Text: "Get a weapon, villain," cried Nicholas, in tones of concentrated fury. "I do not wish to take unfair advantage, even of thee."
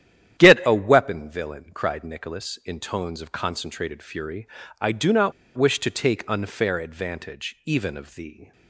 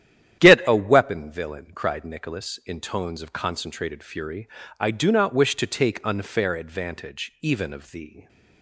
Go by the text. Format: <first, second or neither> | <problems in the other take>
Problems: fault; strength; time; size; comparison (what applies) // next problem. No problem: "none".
second | starts louder than the rest; strong; until 1.4 s; 10.5 dB; strong in the second // pauses between "not" and "wish"; slight; at 5.3 s; 0.25 s long